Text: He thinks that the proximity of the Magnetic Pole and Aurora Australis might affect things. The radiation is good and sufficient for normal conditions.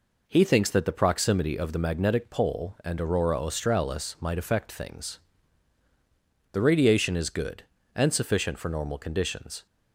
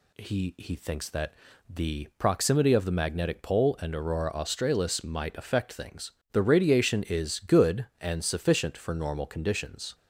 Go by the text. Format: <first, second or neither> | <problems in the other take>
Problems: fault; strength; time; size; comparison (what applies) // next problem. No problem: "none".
first | says "He" twice; at 0.5 s // pauses between "that" and "the"; slight; at 1.3 s; 0.34 s long